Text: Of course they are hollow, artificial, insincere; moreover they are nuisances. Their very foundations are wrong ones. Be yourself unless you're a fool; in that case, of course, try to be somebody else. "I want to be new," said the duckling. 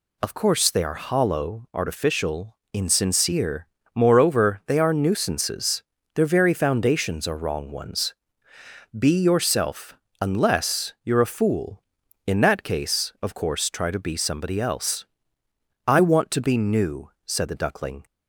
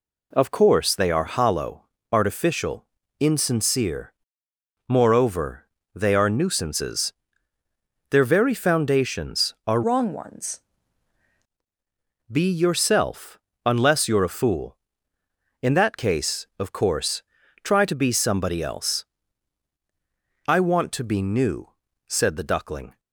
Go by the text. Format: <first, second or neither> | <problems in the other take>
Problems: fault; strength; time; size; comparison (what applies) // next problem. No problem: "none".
first | pauses between "moreover" and "they"; slight; at 5.6 s; 0.26 s long // changes voice from "wrong" to "ones"; from 9.8 to 10.6 s; 0.8 s long // pauses between "yourself" and "unless"; slight; at 13.3 s; 0.24 s long; slight in the first